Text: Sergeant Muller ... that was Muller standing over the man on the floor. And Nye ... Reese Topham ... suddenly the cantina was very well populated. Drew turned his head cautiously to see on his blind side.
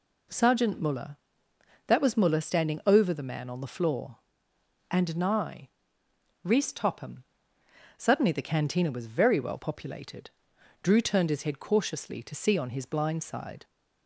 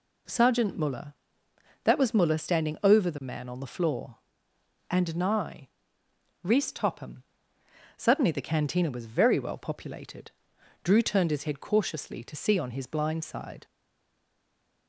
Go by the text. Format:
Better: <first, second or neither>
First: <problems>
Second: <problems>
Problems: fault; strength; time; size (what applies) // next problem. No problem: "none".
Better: first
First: none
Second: stays silent after the last word; noticeable; from 13.6 s on; 1.2 s long